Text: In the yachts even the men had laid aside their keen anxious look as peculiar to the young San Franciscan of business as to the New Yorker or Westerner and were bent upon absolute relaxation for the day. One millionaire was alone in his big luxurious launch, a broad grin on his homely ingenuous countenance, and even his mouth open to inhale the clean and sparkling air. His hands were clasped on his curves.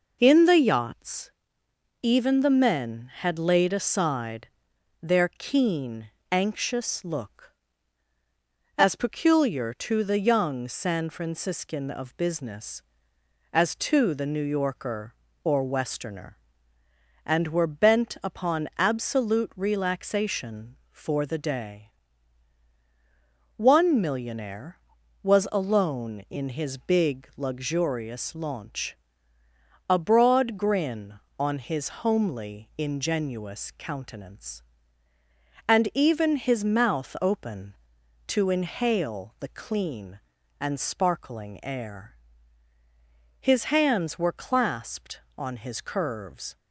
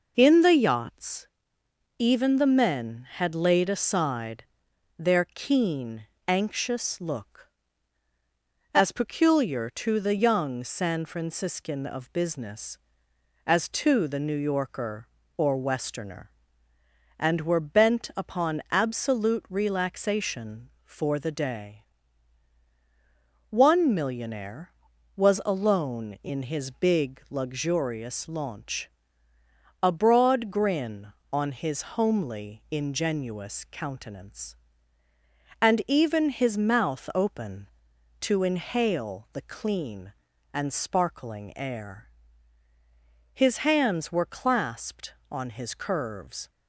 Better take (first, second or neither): neither